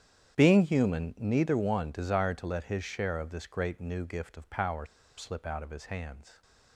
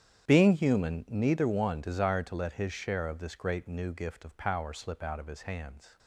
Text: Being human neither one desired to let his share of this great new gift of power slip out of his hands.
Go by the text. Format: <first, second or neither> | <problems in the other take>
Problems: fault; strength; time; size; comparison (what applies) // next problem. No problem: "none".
second | starts louder than the rest; strong; until 1.4 s; 9.5 dB; strong in the second // pauses between "power" and "slip"; slight; at 4.8 s; 0.32 s long